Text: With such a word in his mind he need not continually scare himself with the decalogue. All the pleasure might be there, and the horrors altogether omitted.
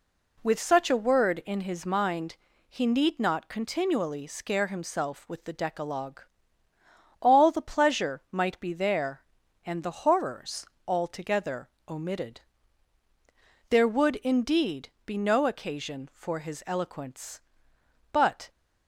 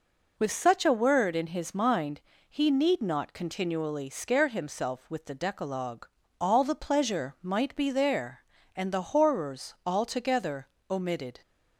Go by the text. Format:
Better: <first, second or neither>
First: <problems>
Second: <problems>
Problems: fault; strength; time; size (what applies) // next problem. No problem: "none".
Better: second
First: pauses between "mind" and "he"; slight; at 2.3 s; 0.34 s long // pauses between "horrors" and "altogether"; slight; at 10.6 s; 0.20 s long // pauses between "altogether" and "omitted"; slight; at 11.6 s; 0.18 s long // goes on to say "There would indeed be no occasion for his eloquence but"; strong; from 13.6 s on; 4.8 s long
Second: pauses between "mind" and "he"; slight; at 2.2 s; 0.26 s long // pauses between "altogether" and "omitted"; slight; at 10.6 s; 0.24 s long